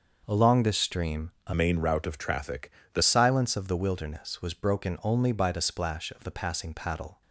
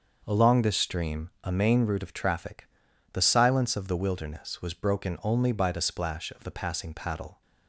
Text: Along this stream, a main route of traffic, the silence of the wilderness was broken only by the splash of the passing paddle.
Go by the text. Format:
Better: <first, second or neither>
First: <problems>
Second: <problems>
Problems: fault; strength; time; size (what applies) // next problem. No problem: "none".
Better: second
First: starts louder than the rest; until 1.2 s; 6 dB // changes voice from "main" to "the"; from 1.5 to 3.0 s; 1.5 s long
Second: starts louder than the rest; until 1.2 s; 6 dB